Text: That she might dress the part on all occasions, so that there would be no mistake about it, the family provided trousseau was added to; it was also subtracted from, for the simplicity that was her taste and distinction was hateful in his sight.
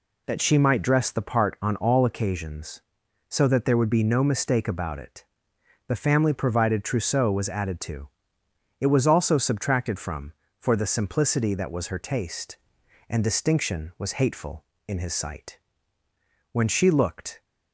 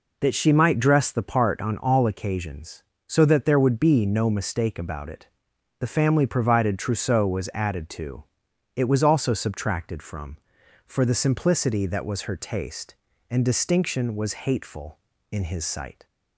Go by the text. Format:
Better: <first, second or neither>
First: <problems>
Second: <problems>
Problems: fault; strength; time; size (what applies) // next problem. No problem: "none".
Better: second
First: goes on to say "When she looked"; noticeable; from 16.5 s on; 0.90 s long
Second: none